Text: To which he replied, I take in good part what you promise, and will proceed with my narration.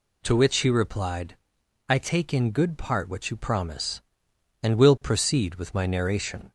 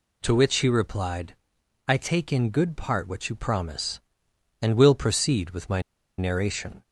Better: first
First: none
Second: pauses between "my" and "narration"; at 5.7 s; 0.38 s long

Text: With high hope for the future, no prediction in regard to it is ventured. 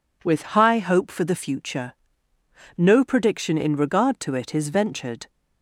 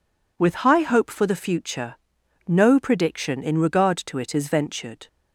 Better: neither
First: none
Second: none

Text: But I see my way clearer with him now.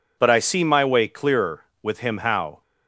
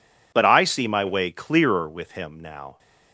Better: second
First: says "how" for "now"; at 2.1 s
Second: none

